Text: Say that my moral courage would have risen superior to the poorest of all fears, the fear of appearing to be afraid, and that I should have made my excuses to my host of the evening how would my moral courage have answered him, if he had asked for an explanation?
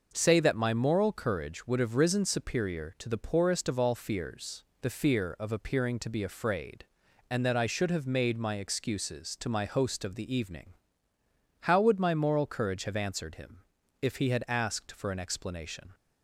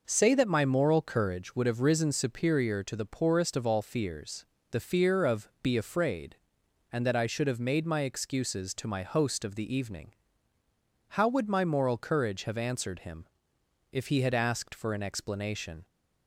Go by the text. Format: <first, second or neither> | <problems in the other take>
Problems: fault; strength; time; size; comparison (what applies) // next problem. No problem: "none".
first | skips "appearing to"; at 5.5 s // pauses between "evening" and "how"; noticeable; at 10.1 s; 0.96 s long; noticeable in the first